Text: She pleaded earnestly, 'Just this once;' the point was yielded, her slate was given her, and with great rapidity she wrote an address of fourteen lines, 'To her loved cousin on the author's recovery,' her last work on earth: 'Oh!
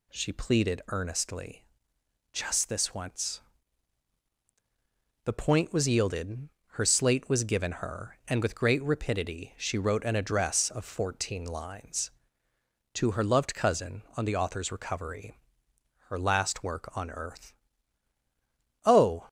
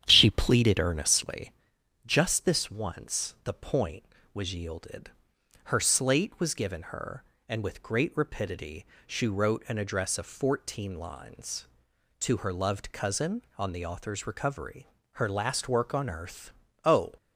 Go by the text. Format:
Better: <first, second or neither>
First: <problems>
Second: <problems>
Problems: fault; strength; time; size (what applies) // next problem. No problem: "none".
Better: first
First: none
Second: starts louder than the rest; strong; until 1.6 s; 9.5 dB // pauses between "rapidity" and "she"; slight; at 8.8 s; 0.20 s long